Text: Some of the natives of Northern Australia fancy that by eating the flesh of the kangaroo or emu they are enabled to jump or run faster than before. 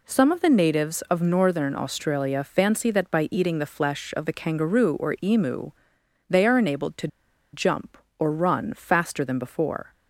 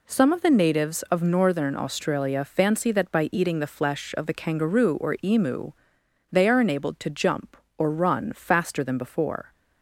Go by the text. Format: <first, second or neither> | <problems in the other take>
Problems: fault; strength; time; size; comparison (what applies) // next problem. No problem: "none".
second | pauses between "emu" and "they"; noticeable; at 5.7 s; 0.56 s long; noticeable in the second // pauses between "to" and "jump"; at 7.0 s; 0.45 s long